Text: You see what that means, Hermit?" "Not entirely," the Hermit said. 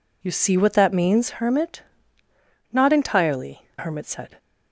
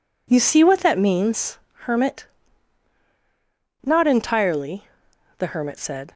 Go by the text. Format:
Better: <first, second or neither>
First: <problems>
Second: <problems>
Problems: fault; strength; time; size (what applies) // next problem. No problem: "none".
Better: second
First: skips "the"; at 3.7 s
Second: none